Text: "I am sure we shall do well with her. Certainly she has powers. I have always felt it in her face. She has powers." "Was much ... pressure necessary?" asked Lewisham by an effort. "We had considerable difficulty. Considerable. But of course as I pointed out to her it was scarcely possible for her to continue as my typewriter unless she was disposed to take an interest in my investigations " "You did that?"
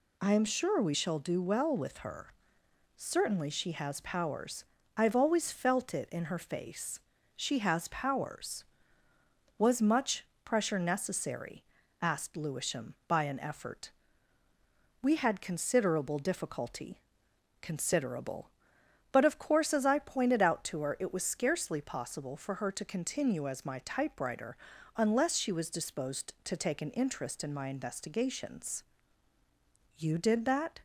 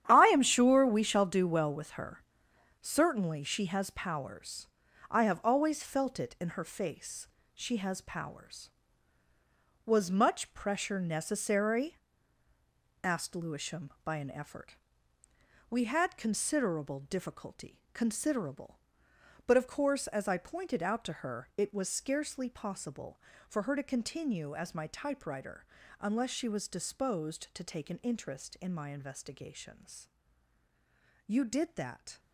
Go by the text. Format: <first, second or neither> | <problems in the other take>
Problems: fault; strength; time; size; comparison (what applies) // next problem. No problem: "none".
first | gets quieter; strong; throughout; 14.5 dB // pauses between "typewriter" and "unless"; slight; at 25.6 s; 0.36 s long; also in the first